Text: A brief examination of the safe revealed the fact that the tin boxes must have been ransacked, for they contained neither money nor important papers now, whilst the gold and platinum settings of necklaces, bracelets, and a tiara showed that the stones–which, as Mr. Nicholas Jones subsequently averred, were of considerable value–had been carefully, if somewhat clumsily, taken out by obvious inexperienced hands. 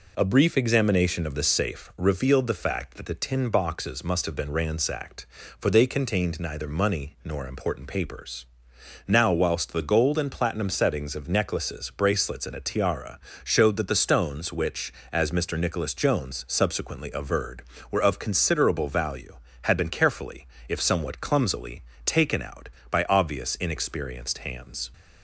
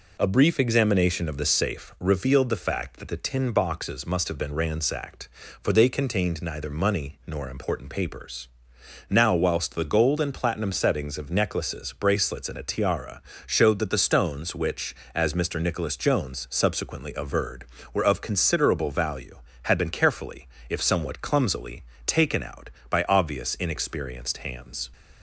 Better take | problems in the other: neither | pauses between "papers" and "now"; noticeable; the same in both // pauses between "tiara" and "showed"; slight; the same in both

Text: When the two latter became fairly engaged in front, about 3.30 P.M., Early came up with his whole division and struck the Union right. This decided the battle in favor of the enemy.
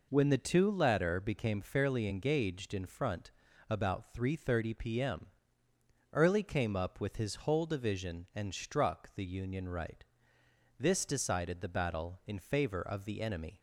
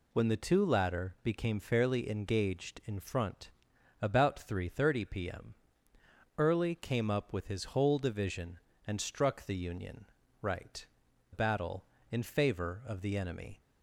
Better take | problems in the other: first | pauses between "Union" and "right"; slight; at 10.0 s; 0.34 s long // skips "This decided the"; at 11.0 s

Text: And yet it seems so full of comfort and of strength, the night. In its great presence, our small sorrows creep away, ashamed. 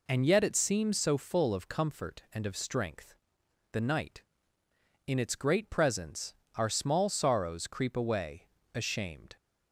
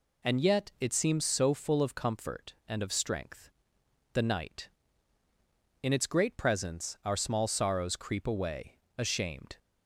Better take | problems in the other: neither | none

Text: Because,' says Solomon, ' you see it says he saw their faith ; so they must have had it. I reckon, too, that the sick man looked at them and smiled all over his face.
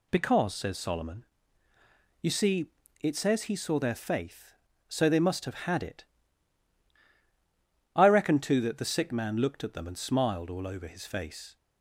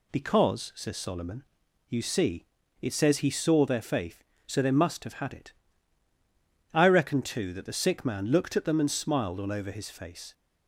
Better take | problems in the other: neither | pauses between "see" and "it"; slight; the same in both

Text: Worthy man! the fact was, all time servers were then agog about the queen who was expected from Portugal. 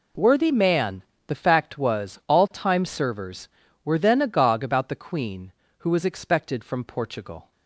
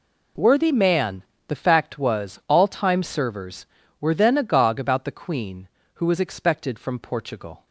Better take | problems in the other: neither | none

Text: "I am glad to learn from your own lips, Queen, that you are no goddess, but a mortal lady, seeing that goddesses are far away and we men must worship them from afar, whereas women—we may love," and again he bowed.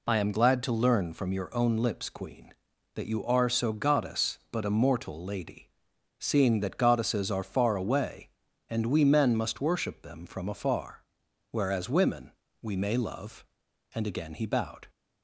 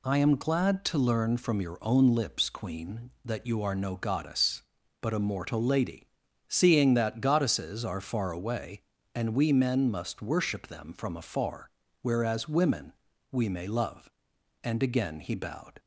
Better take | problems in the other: second | says "so" for "no"; at 3.5 s

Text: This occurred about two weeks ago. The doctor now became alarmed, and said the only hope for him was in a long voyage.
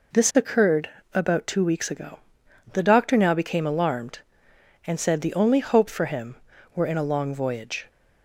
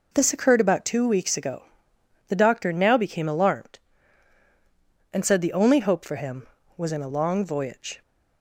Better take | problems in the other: second | pauses between "occurred" and "about"; slight; at 0.8 s; 0.26 s long // says "were" for "was"; at 6.7 s

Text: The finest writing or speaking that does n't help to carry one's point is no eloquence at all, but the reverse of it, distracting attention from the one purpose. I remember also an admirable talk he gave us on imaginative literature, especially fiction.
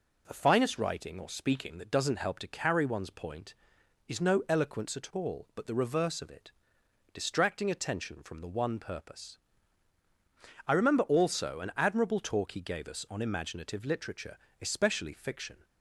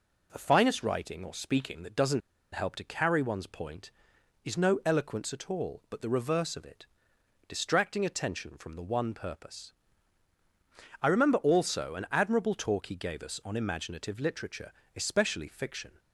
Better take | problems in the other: first | pauses between "n't" and "help"; slight; at 2.2 s; 0.34 s long

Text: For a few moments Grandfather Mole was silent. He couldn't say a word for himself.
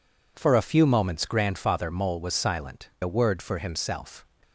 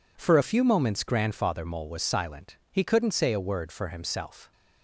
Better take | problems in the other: second | skips "He couldn't say"; at 2.9 s

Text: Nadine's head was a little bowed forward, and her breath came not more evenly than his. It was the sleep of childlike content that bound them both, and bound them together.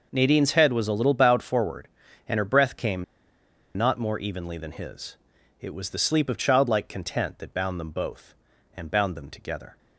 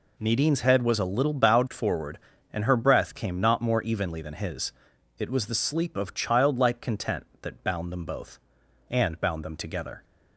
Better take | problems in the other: second | pauses between "came" and "not"; noticeable; at 3.0 s; 0.73 s long

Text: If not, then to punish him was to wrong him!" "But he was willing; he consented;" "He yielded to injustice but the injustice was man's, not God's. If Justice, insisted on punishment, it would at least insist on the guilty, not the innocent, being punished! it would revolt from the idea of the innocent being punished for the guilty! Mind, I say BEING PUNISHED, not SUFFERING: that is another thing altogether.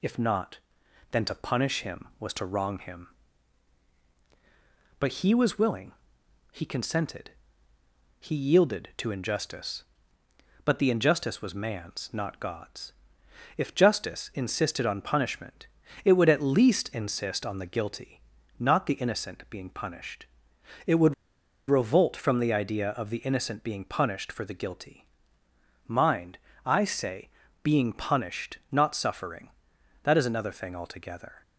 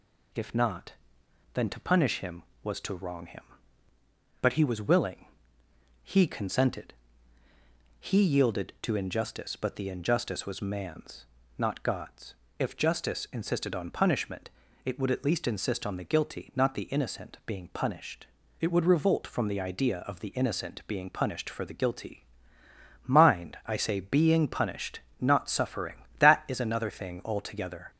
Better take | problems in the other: second | pauses between "would" and "revolt"; noticeable; at 21.1 s; 0.53 s long // pauses between "say" and "BEING"; slight; at 27.2 s; 0.36 s long

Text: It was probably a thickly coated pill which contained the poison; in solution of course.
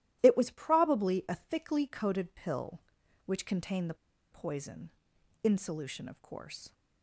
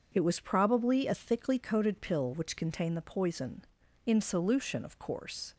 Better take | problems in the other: second | starts louder than the rest; strong; until 1.2 s; 13.5 dB; also in the second // pauses between "the" and "poison"; at 3.9 s; 0.37 s long

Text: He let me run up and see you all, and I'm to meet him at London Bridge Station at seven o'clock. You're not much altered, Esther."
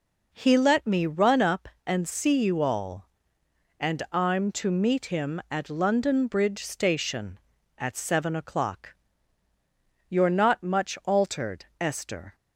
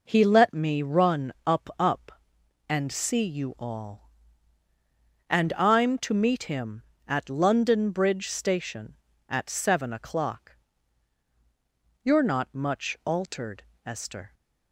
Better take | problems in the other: first | says "up" twice; at 1.7 s

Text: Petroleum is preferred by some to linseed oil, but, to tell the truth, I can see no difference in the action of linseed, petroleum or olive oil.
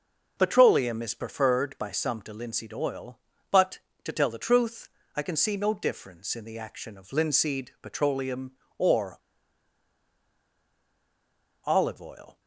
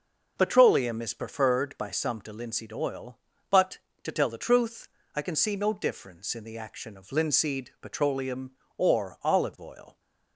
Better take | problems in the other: second | pauses between "or" and "olive"; strong; at 9.1 s; 2.4 s long

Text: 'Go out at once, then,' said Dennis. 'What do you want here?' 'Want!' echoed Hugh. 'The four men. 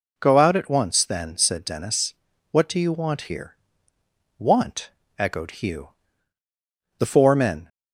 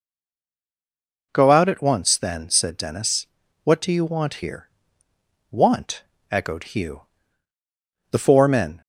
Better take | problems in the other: first | stays silent before the first word; noticeable; until 1.3 s; 1.3 s long

